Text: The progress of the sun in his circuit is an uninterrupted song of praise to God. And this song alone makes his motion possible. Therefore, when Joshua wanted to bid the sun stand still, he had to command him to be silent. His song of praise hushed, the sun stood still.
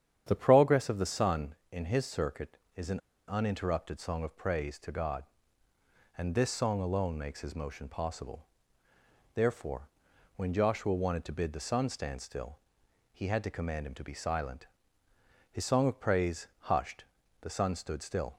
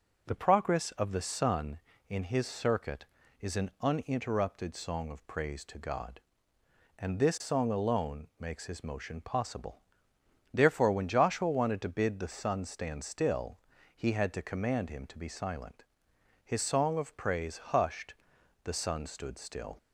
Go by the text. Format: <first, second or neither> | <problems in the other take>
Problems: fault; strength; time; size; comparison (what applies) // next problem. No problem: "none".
second | starts louder than the rest; strong; until 1.2 s; 9 dB // pauses between "an" and "uninterrupted"; slight; at 2.9 s; 0.29 s long